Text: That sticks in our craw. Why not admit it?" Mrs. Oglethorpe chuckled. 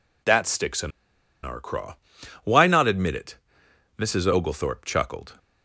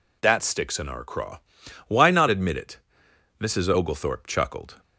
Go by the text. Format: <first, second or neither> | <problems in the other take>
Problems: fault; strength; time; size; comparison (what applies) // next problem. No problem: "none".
second | pauses between "in" and "our"; noticeable; at 0.9 s; 0.53 s long